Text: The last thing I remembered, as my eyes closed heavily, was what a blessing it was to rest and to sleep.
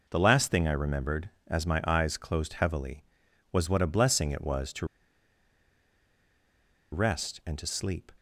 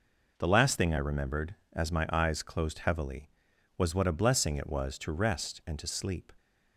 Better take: second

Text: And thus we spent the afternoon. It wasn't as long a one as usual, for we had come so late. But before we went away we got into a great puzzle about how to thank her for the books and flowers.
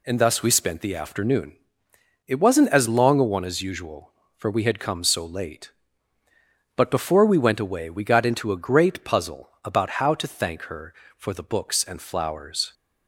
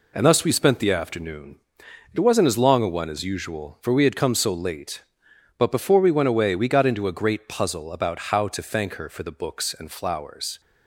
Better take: neither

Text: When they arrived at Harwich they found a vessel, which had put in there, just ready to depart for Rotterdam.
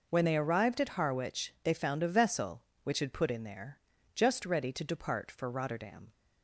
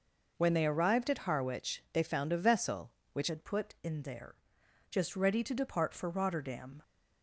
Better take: first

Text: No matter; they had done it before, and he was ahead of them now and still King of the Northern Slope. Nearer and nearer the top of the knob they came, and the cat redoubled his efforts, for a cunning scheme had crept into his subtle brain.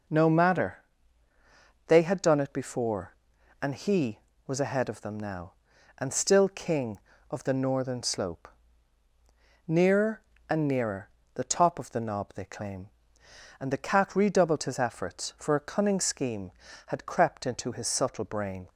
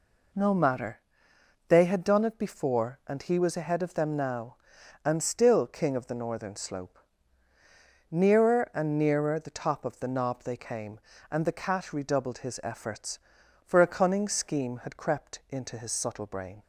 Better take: second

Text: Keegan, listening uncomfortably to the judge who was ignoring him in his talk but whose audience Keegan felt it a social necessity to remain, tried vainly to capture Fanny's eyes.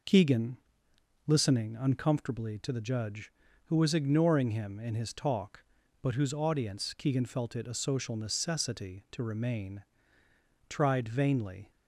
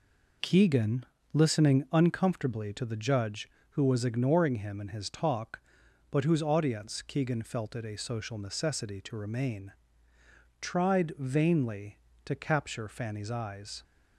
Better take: second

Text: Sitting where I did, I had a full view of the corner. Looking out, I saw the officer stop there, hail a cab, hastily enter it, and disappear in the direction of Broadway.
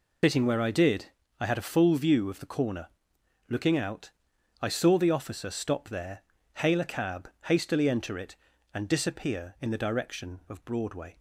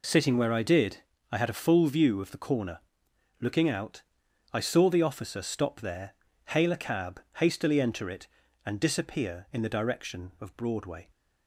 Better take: second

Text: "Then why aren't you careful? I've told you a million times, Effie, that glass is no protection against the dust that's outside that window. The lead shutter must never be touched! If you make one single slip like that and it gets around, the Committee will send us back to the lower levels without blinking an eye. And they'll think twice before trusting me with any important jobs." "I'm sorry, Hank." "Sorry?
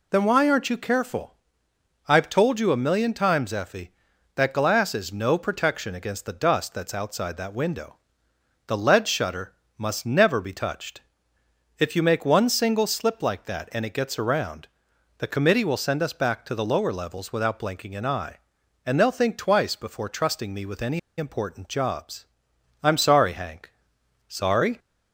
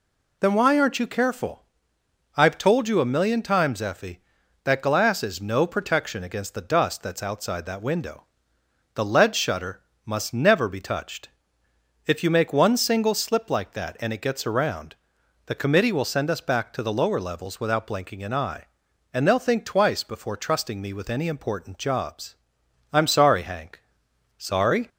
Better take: second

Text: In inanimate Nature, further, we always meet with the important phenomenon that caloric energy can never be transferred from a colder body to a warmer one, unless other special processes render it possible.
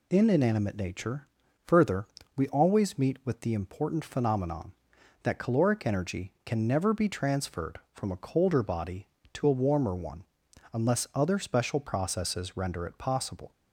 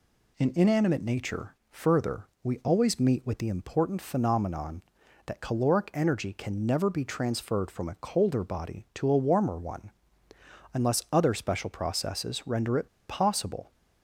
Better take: first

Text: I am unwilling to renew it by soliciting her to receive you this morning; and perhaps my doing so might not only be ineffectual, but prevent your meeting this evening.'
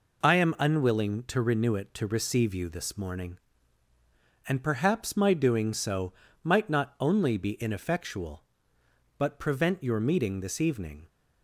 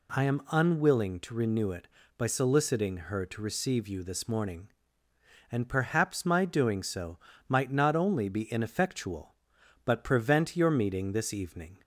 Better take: second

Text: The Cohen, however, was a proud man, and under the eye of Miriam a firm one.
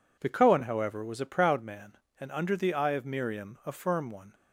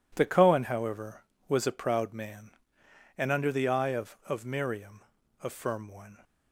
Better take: first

